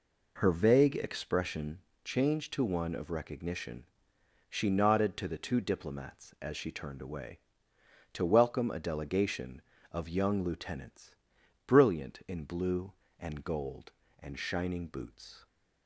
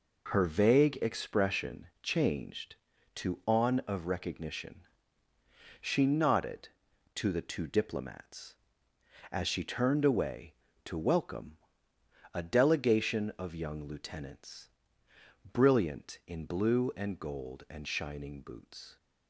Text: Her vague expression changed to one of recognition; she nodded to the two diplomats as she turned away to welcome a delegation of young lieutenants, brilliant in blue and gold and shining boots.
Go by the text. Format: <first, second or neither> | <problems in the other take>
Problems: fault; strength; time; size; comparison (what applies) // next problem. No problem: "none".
first | pauses between "expression" and "changed"; slight; at 1.8 s; 0.16 s long; slight in the first // says "on" for "one"; at 3.4 s // pauses between "welcome" and "a"; noticeable; at 11.5 s; 0.74 s long